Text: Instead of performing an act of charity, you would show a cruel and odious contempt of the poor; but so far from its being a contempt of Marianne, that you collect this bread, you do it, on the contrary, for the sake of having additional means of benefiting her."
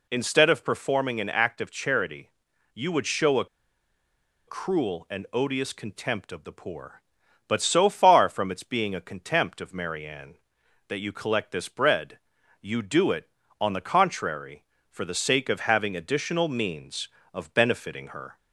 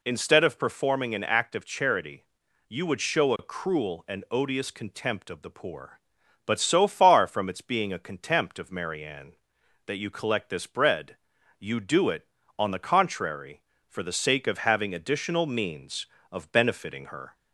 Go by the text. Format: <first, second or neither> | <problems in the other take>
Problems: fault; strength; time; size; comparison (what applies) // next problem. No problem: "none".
second | pauses between "a" and "cruel"; at 3.4 s; 1.0 s long